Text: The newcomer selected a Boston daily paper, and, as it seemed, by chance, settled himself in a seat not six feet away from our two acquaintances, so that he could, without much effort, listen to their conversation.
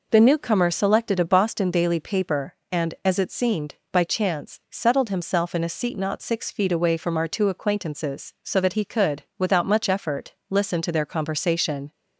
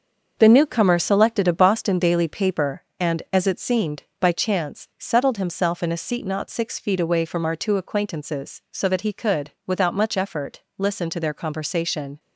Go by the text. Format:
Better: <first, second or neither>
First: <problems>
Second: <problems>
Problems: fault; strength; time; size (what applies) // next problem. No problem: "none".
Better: first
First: none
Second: gets quieter; throughout; 7 dB